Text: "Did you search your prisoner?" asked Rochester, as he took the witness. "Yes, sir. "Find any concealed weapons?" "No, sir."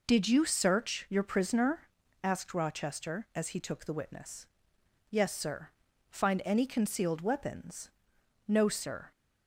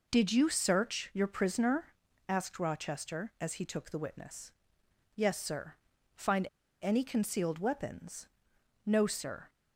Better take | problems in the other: first | pauses between "Find" and "any"; slight; at 6.4 s; 0.34 s long

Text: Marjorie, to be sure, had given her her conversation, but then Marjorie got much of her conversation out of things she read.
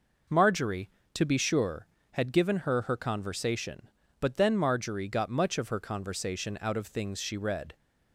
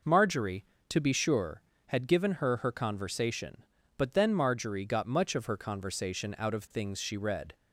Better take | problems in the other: neither | none

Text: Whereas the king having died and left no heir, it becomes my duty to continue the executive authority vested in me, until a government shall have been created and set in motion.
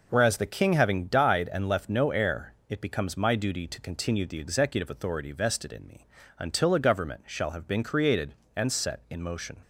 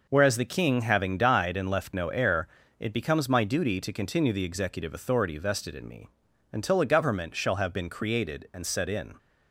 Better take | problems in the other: first | stops before "motion"; at 9.1 s

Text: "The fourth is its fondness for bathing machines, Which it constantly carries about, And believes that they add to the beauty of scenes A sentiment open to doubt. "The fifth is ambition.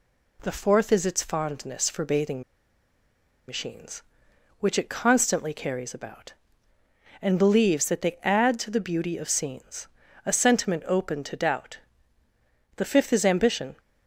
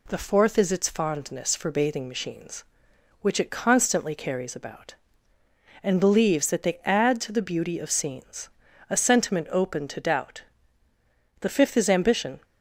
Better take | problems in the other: second | pauses between "bathing" and "machines"; at 2.4 s; 1.0 s long // pauses between "scenes" and "A"; at 9.8 s; 0.38 s long; also in the second

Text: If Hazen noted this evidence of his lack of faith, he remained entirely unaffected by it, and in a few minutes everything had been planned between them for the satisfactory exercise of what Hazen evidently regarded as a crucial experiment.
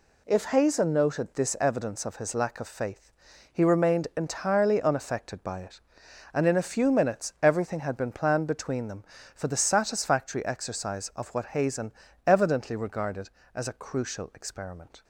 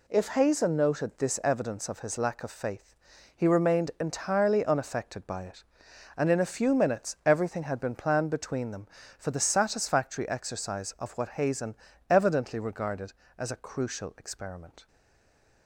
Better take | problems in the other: first | pauses between "Hazen" and "evidently"; slight; at 11.7 s; 0.34 s long; slight in the first // stays silent after the last word; slight; from 14.8 s on; 0.8 s long

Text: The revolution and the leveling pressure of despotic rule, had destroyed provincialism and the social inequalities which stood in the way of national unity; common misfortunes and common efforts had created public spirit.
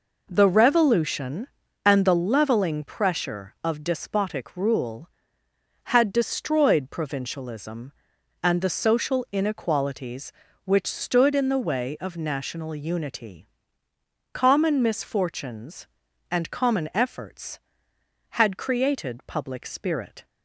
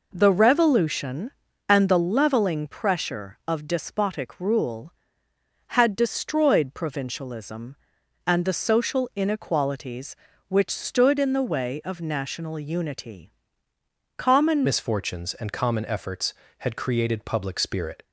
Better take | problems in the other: first | changes voice at "misfortunes"; from 14.6 s on; 3.4 s long

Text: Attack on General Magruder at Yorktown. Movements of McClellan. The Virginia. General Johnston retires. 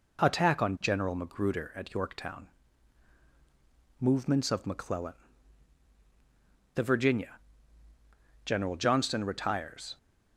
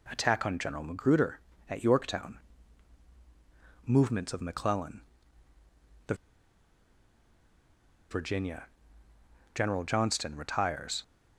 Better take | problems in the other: first | pauses between "The" and "Virginia"; strong; at 6.1 s; 1.9 s long

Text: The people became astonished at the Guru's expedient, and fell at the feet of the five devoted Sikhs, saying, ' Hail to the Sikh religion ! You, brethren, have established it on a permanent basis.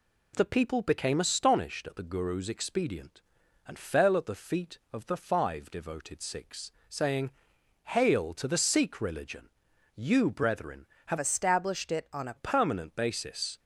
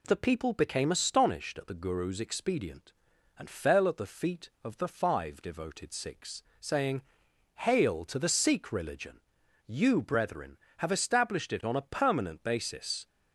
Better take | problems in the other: second | changes voice from "established" to "a"; from 11.1 to 12.3 s; 1.2 s long

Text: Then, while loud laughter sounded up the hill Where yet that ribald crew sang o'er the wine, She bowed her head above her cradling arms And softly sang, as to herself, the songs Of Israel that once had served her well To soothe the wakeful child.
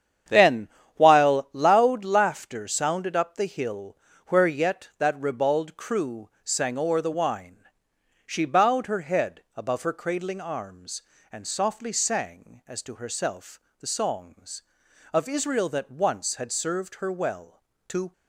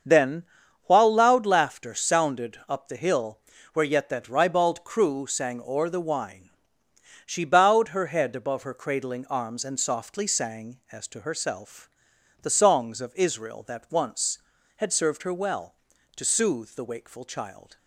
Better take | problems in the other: second | starts louder than the rest; strong; until 1.5 s; 8.5 dB; also in the second // pauses between "hill" and "Where"; slight; at 3.9 s; 0.32 s long; slight in the second // stops before "soothe the wakeful child"; at 18.1 s

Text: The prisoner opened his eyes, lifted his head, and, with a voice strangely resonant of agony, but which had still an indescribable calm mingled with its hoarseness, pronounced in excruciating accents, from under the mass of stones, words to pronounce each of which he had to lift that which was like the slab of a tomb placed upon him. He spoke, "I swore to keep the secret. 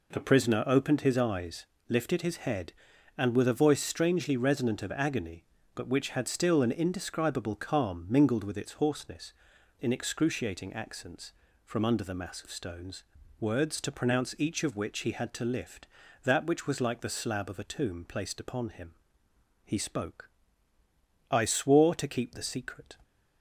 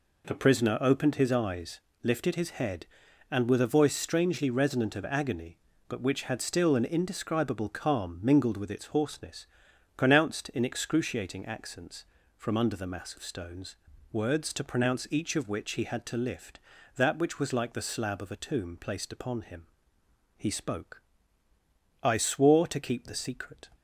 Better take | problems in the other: second | skips "pronounced"; at 9.5 s

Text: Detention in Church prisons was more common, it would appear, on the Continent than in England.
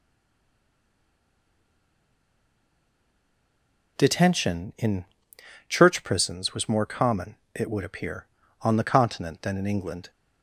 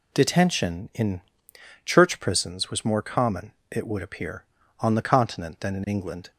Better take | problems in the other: second | stays silent before the first word; strong; until 3.9 s; 3.9 s long // pauses between "in" and "Church"; noticeable; at 5.0 s; 0.64 s long; noticeable in the second

